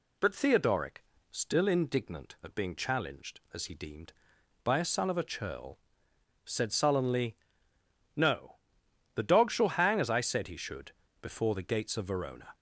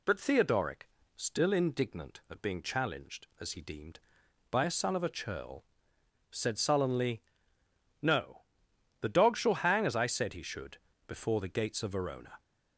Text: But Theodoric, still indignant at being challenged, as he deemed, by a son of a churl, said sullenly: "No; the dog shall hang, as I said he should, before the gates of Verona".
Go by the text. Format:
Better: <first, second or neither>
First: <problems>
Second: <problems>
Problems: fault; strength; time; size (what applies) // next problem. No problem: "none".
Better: neither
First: none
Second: none